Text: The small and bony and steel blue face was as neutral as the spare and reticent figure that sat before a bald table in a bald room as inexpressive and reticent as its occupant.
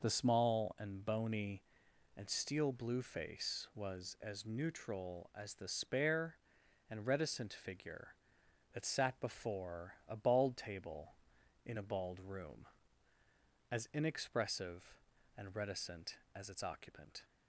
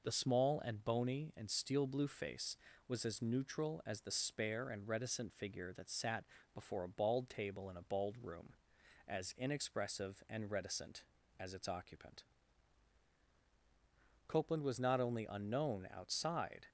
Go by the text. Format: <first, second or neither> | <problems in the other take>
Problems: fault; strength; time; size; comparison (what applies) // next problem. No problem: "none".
first | pauses between "sat" and "before"; slight; at 6.2 s; 0.28 s long // goes on to say "Copeland was not only unknown outside"; strong; from 14.2 s on; 2.4 s long